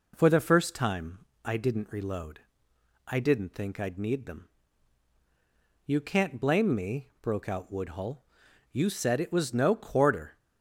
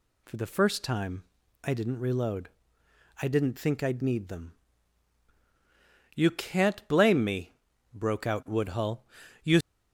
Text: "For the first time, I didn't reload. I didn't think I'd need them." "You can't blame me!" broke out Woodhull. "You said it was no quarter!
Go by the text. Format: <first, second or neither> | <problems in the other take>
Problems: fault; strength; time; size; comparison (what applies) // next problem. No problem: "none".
first | stops before "said it was no quarter"; at 9.6 s